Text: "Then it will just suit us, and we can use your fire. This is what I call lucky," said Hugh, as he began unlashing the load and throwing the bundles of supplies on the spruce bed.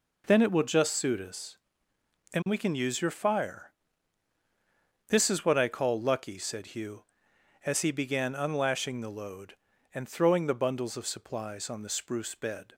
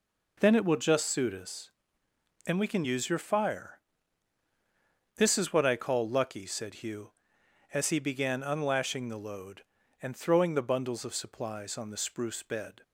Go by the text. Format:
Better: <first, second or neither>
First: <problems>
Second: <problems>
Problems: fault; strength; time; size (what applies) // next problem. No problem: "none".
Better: neither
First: none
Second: none